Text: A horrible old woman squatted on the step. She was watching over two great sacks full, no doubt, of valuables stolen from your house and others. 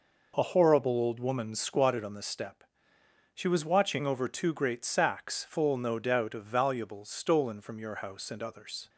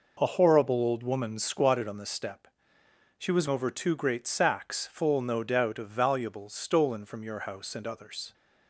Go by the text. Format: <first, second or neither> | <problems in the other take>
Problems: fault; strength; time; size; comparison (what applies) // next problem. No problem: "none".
first | skips "watching"; at 3.4 s